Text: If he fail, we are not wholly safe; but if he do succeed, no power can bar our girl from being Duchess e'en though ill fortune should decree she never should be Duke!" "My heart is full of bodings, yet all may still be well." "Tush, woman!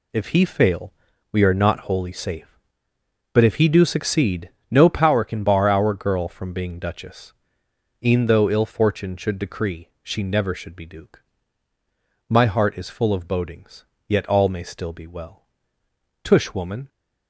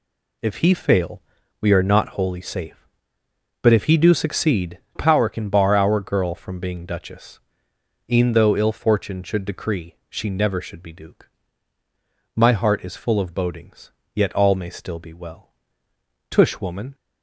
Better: first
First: pauses between "Duchess" and "e'en"; noticeable; at 7.3 s; 0.72 s long // pauses between "decree" and "she"; slight; at 9.8 s; 0.16 s long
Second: skips "no"; at 4.8 s // pauses between "Duchess" and "e'en"; noticeable; at 7.3 s; 0.72 s long // pauses between "decree" and "she"; slight; at 9.9 s; 0.16 s long

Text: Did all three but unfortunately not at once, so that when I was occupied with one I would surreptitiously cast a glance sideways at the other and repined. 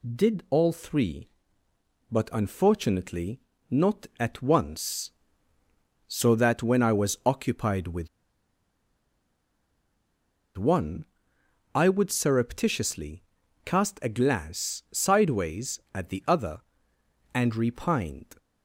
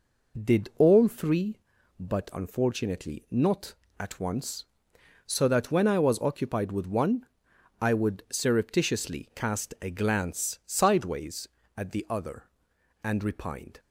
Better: second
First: pauses between "unfortunately" and "not"; slight; at 3.3 s; 0.32 s long // pauses between "with" and "one"; strong; at 8.0 s; 2.4 s long // pauses between "one" and "I"; noticeable; at 11.0 s; 0.70 s long // pauses between "surreptitiously" and "cast"; at 13.2 s; 0.44 s long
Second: pauses between "one" and "I"; noticeable; at 7.2 s; 0.54 s long

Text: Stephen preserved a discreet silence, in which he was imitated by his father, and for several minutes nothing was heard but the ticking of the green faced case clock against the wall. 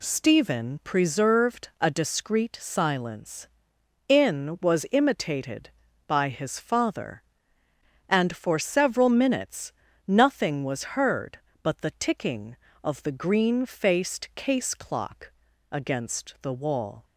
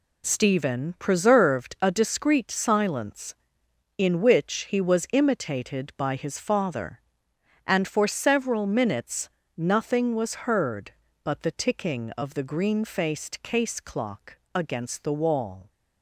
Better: second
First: skips "which he"; at 4.5 s // pauses between "minutes" and "nothing"; slight; at 9.7 s; 0.36 s long // pauses between "clock" and "against"; at 15.3 s; 0.38 s long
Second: pauses between "minutes" and "nothing"; slight; at 9.2 s; 0.30 s long // pauses between "clock" and "against"; slight; at 14.3 s; 0.18 s long

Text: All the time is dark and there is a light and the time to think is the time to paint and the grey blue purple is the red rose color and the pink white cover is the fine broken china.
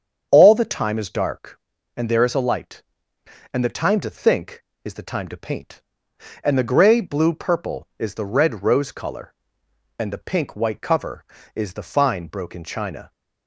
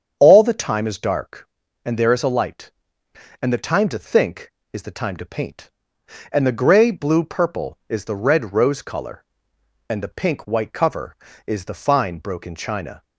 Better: neither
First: starts louder than the rest; strong; until 1.3 s; 7.5 dB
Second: starts louder than the rest; strong; until 1.2 s; 7.5 dB

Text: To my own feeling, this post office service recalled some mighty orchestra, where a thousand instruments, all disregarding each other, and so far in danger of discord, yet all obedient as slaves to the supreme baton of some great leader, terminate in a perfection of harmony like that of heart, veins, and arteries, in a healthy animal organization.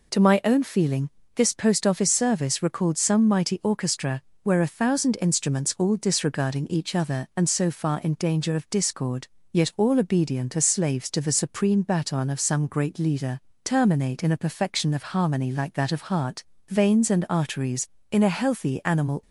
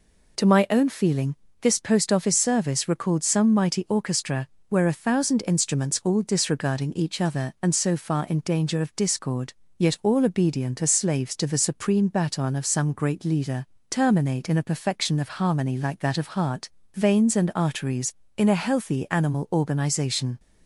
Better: second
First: stops before "organization"; at 19.2 s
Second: none

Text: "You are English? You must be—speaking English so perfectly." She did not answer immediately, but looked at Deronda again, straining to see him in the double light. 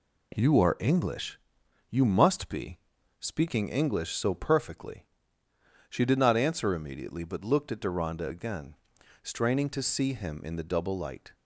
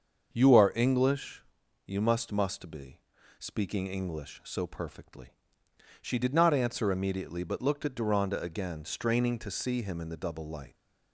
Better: first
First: none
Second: starts louder than the rest; until 1.3 s; 6.5 dB // says "must" twice; at 2.3 s

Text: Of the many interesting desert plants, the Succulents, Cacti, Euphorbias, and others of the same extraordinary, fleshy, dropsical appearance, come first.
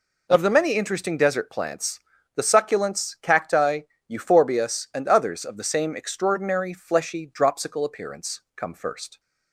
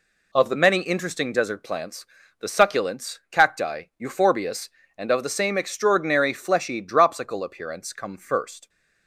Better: first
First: none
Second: skips "others"; at 5.1 s

